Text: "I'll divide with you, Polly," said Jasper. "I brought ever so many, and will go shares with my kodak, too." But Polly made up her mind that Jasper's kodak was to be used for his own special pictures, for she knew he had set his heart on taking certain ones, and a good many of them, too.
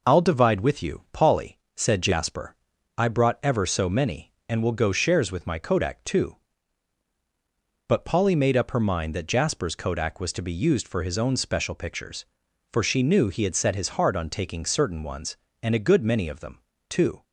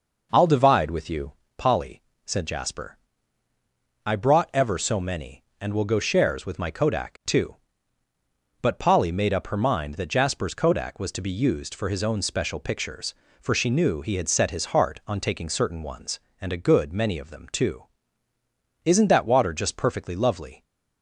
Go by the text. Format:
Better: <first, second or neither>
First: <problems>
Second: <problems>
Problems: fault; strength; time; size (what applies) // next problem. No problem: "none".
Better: first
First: none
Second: goes on to say "Isn't that water just perfectly lovely"; strong; from 18.8 s on; 1.8 s long